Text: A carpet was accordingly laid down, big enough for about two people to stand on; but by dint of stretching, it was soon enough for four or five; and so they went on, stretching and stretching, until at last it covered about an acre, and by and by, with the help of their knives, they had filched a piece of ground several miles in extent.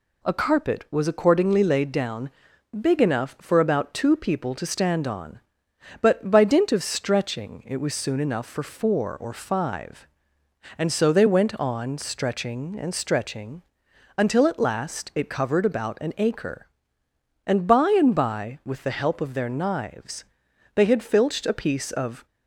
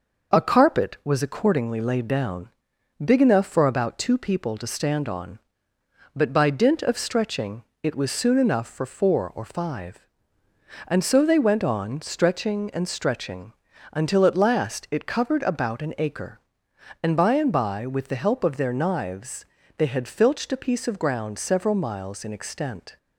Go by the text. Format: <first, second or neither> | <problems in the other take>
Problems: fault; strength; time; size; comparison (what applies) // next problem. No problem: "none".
second | stops before "ground several miles in extent"; at 22.2 s